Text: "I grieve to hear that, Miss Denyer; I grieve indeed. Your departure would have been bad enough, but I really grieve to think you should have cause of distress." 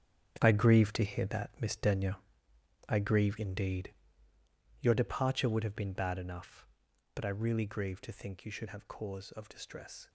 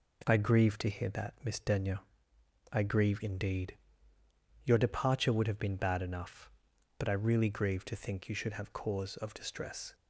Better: second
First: gets quieter; strong; throughout; 12 dB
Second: none

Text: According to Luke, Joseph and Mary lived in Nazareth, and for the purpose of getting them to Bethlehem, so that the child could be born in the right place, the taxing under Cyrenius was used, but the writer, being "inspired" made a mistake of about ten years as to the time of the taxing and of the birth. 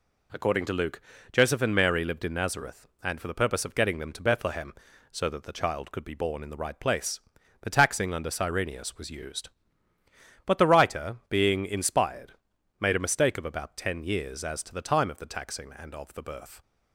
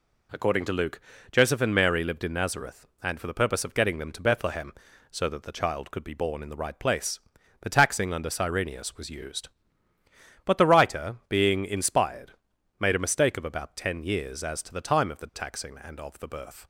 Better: neither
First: pauses between "inspired" and "made"; noticeable; at 12.3 s; 0.46 s long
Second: pauses between "inspired" and "made"; noticeable; at 12.3 s; 0.46 s long

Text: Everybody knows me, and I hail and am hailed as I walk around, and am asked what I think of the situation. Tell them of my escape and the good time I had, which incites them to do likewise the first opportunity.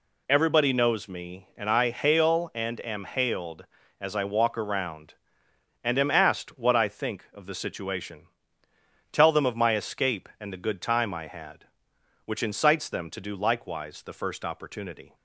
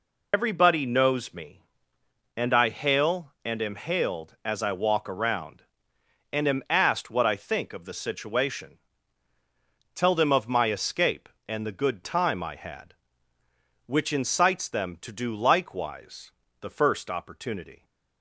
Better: first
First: none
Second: loses the start of "Everybody"; at 0.3 s; 80 ms // pauses between "likewise" and "the"; slight; at 16.3 s; 0.30 s long

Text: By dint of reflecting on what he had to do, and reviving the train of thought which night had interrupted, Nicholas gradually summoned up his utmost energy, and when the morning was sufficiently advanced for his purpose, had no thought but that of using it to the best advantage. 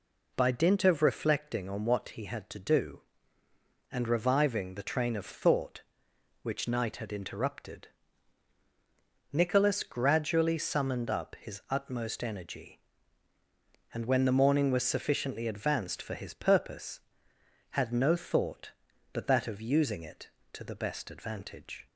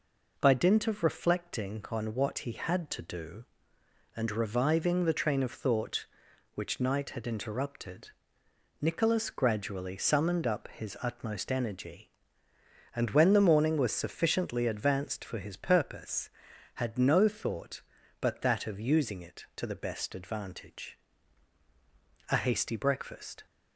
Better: first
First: none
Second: goes on to say "A hasty breakfast"; noticeable; from 22.2 s on; 1.1 s long

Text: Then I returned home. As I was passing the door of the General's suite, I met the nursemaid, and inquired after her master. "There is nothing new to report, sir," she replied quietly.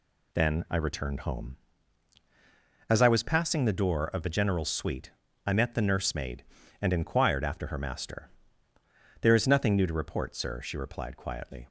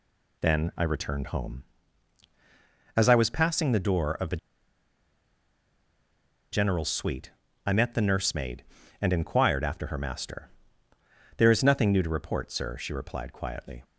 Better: first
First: none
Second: pauses between "the" and "General's"; strong; at 4.3 s; 2.1 s long

